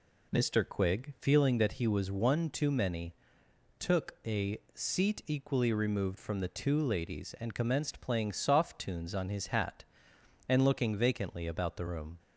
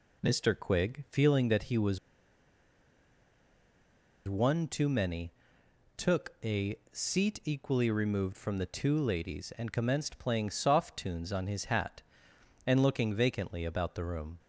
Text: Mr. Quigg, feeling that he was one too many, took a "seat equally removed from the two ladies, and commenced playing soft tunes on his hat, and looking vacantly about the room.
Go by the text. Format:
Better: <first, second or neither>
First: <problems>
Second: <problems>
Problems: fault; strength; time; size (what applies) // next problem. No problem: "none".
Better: first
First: pauses between "a" and "seat"; slight; at 4.5 s; 0.16 s long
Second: pauses between "was" and "one"; strong; at 1.9 s; 2.3 s long // pauses between "a" and "seat"; slight; at 6.7 s; 0.16 s long